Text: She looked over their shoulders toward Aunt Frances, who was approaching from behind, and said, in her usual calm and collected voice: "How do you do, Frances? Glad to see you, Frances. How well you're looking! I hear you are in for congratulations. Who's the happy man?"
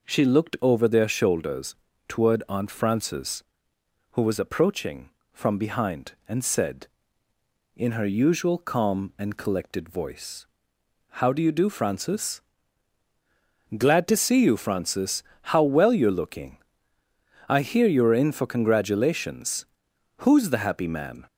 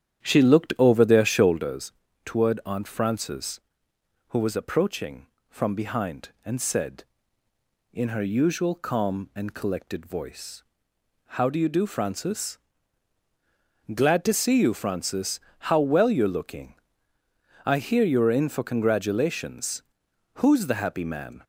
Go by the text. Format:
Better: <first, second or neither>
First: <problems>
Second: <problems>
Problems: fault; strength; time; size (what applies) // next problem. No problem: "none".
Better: first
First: pauses between "shoulders" and "toward"; slight; at 1.7 s; 0.34 s long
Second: starts louder than the rest; strong; until 1.8 s; 9.5 dB // pauses between "shoulders" and "toward"; slight; at 1.9 s; 0.34 s long